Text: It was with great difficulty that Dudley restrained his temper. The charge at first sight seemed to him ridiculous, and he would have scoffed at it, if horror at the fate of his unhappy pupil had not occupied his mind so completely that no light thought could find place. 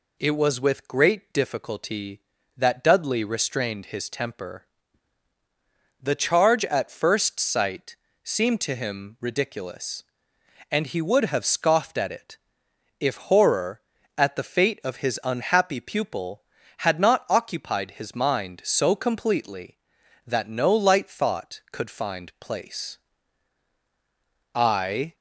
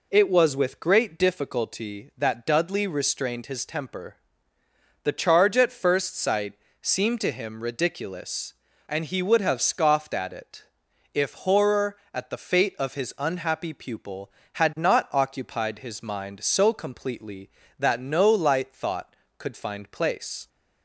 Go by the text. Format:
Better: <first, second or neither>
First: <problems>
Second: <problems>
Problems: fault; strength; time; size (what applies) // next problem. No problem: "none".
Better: second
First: pauses between "sight" and "seemed"; slight; at 7.9 s; 0.28 s long // goes on to say "I"; from 24.5 s on; 0.60 s long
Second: pauses between "sight" and "seemed"; slight; at 6.5 s; 0.28 s long